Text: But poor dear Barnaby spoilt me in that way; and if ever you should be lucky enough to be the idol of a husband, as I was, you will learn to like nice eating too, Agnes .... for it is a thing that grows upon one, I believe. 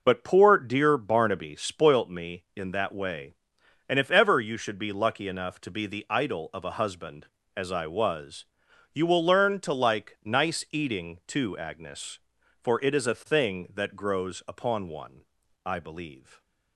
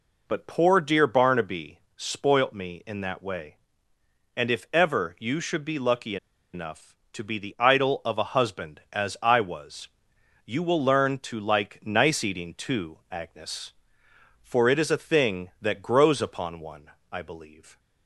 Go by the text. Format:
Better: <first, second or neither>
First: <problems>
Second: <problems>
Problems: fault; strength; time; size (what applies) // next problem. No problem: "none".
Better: first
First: none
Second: pauses between "Barnaby" and "spoilt"; slight; at 1.7 s; 0.16 s long // pauses between "lucky" and "enough"; at 6.1 s; 0.37 s long